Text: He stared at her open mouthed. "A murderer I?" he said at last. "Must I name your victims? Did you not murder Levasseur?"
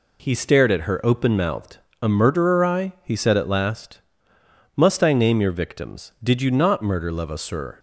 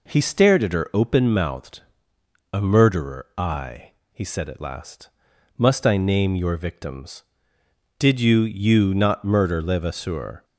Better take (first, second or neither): first